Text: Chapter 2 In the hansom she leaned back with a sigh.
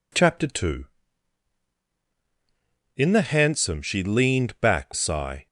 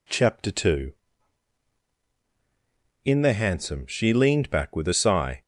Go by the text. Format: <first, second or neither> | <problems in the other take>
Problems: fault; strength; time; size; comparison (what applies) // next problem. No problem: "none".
second | skips "with a"; at 4.9 s